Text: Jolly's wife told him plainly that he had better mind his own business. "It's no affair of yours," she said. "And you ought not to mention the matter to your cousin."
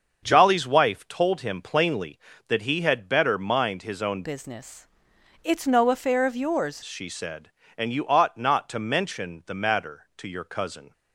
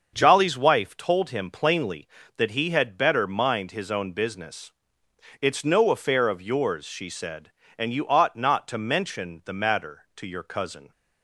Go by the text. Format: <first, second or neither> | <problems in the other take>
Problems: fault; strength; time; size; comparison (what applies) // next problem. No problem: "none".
second | starts louder than the rest; until 1.2 s; 7 dB; also in the second // changes voice from "business" to "yours"; from 4.2 to 6.8 s; 2.6 s long